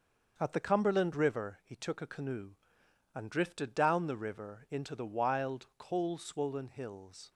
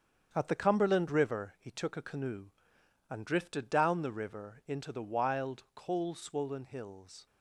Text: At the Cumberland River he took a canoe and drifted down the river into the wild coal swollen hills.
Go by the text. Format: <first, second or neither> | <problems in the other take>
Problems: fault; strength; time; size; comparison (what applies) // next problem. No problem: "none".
first | gets quieter; noticeable; throughout; 6 dB // starts louder than the rest; strong; until 1.3 s; 7.5 dB; also in the first